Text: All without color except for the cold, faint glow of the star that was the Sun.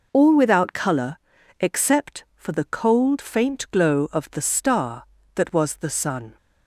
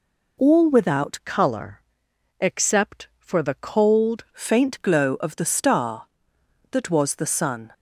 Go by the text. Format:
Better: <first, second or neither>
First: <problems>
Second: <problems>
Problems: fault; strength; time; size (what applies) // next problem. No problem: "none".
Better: first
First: pauses between "color" and "except"; at 1.1 s; 0.42 s long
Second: changes voice from "color" to "cold"; from 1.2 to 4.2 s; 3.0 s long // pauses between "color" and "except"; noticeable; at 1.8 s; 0.58 s long